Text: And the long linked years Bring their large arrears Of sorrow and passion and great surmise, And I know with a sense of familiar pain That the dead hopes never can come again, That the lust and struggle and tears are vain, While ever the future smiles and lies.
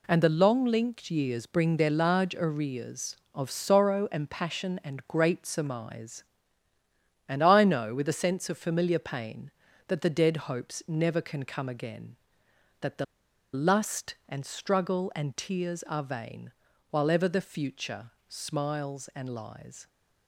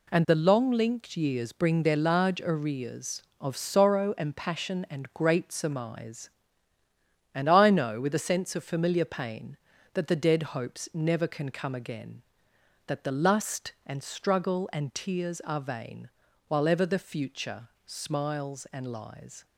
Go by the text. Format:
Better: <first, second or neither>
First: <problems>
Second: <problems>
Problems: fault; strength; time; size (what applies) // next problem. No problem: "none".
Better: second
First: pauses between "the" and "lust"; noticeable; at 13.0 s; 0.48 s long // pauses between "future" and "smiles"; slight; at 18.1 s; 0.16 s long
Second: pauses between "future" and "smiles"; slight; at 17.6 s; 0.16 s long